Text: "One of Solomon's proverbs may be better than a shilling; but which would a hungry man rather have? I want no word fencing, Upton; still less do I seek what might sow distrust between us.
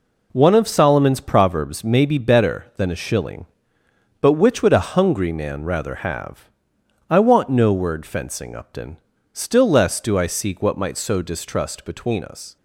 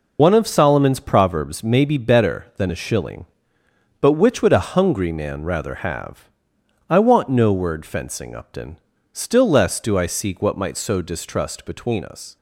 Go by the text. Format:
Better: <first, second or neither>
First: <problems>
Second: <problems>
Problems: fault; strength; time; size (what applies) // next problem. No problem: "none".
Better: first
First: none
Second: loses the start of "One"; at 0.1 s; 80 ms